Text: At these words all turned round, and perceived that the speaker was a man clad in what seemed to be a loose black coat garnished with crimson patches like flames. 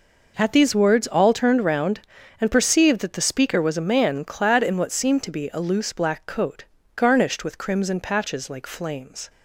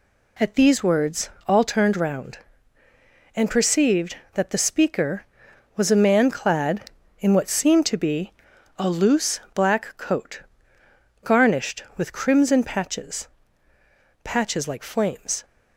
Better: first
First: pauses between "coat" and "garnished"; slight; at 6.6 s; 0.32 s long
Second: pauses between "words" and "all"; slight; at 1.2 s; 0.18 s long // pauses between "be" and "a"; at 8.3 s; 0.44 s long // pauses between "coat" and "garnished"; noticeable; at 10.4 s; 0.82 s long // says "patches" twice; at 14.2 s

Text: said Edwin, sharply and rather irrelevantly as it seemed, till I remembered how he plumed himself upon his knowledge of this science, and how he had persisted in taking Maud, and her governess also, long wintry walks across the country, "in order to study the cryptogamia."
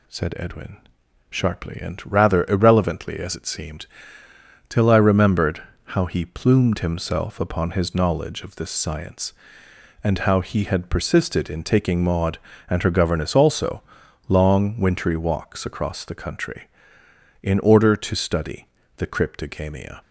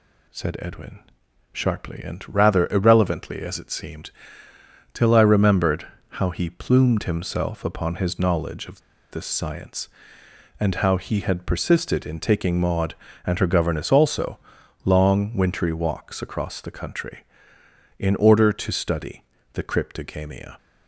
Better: first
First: pauses between "remembered" and "how"; slight; at 5.6 s; 0.30 s long // pauses between "study" and "the"; slight; at 18.6 s; 0.30 s long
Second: pauses between "remembered" and "how"; slight; at 5.8 s; 0.30 s long // pauses between "of" and "this"; slight; at 8.7 s; 0.31 s long // pauses between "study" and "the"; slight; at 19.2 s; 0.30 s long

